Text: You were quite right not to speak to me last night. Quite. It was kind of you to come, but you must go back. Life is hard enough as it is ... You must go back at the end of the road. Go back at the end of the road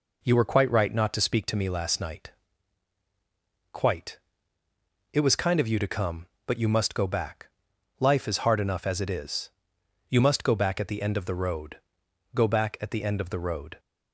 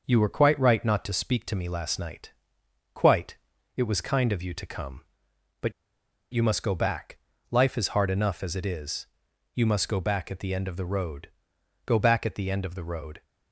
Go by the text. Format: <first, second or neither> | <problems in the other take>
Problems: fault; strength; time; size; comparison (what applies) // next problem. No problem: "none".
first | pauses between "but" and "you"; noticeable; at 5.7 s; 0.60 s long